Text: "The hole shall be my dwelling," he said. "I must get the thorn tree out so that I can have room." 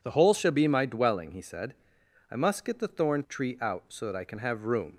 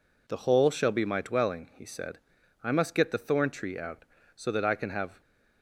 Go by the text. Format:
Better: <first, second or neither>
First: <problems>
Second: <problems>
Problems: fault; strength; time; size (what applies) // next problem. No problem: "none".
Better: first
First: none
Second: stops before "room"; at 5.2 s